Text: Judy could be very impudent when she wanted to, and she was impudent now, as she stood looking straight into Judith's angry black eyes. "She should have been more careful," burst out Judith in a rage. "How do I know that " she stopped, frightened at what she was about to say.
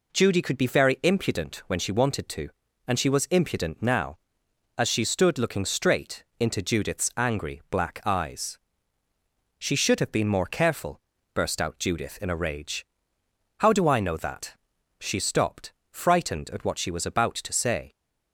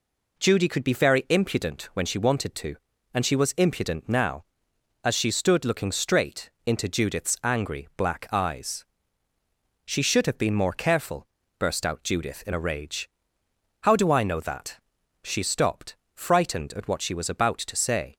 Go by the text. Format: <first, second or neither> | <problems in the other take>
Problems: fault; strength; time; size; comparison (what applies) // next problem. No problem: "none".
neither | pauses between "straight" and "into"; slight; the same in both